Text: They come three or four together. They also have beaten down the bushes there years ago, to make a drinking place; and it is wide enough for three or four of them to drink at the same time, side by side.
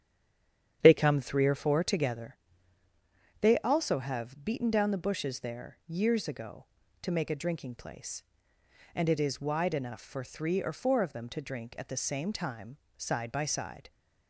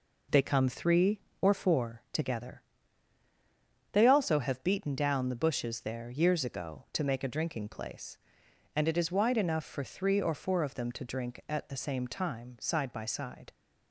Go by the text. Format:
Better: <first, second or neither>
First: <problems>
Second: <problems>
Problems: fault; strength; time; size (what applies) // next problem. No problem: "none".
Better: second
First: stays silent before the first word; slight; until 0.8 s; 0.8 s long // starts louder than the rest; strong; until 1.8 s; 9 dB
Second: none